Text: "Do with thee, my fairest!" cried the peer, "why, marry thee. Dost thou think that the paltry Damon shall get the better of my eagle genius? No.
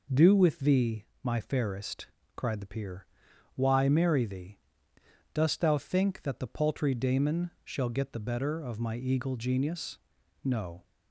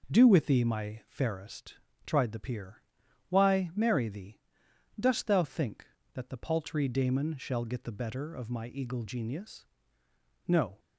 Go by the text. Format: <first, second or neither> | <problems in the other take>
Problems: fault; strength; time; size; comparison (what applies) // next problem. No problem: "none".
first | says "tried" for "cried"; at 2.0 s